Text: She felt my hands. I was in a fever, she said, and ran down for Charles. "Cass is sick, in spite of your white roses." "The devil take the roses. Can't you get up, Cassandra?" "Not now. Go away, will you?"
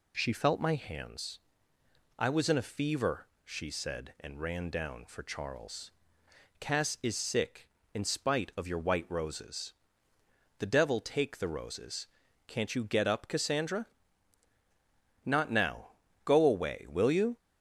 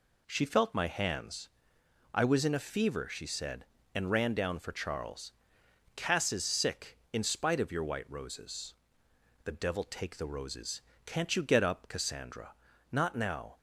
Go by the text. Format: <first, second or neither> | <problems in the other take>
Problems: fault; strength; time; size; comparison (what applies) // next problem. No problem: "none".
first | stops before "Go away will you"; at 13.5 s